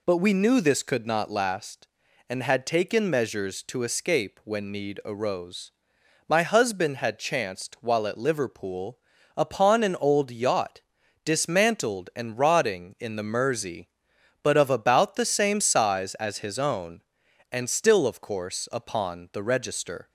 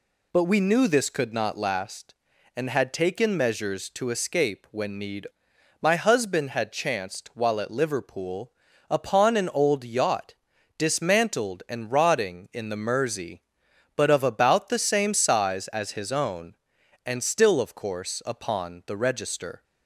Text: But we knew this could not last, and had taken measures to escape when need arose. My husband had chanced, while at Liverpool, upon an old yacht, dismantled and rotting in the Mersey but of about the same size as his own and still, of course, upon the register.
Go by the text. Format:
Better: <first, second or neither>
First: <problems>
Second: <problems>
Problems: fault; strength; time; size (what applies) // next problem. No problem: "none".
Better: first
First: none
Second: skips "arose"; at 5.5 s